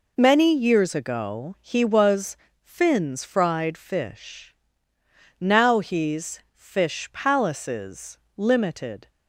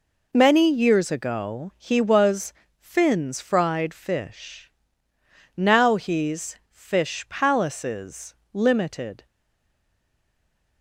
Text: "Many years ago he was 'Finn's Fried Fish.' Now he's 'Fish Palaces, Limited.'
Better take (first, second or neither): first